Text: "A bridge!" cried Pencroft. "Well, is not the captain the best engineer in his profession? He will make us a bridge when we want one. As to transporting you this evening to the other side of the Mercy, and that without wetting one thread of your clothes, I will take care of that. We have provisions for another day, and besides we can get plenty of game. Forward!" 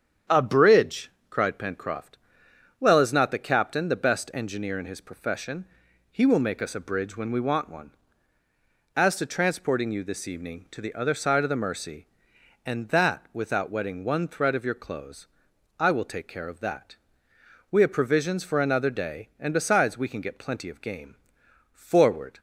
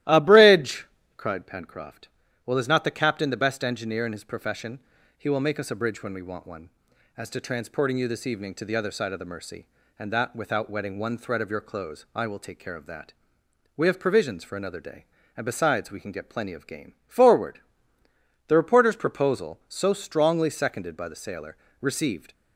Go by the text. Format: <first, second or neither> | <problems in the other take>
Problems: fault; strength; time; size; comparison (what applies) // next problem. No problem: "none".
first | starts louder than the rest; strong; until 1.3 s; 14.5 dB; strong in the first // goes on to say "The reporter's proposal so strongly seconded by the sailor received"; strong; from 18.4 s on; 3.8 s long